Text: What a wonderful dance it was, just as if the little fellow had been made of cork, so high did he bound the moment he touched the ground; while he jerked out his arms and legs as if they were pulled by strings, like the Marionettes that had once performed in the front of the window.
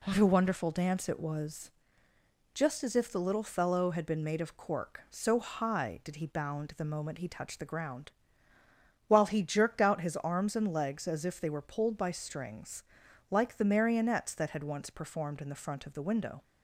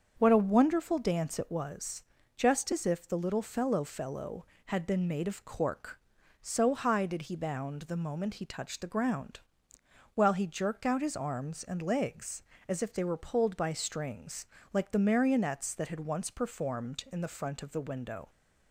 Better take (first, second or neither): first